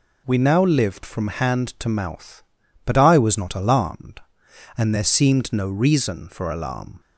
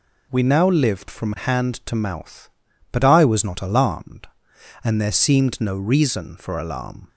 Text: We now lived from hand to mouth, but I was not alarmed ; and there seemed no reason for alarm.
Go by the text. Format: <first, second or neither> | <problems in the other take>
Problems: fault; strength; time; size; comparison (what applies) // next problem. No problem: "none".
neither | none